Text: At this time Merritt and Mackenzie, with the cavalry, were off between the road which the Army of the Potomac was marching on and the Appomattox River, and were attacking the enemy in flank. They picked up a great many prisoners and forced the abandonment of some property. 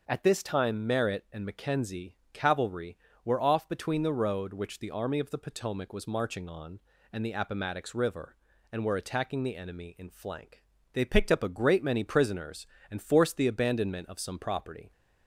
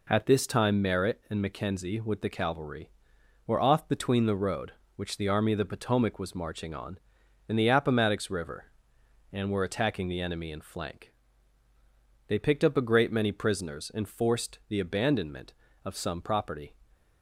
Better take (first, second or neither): second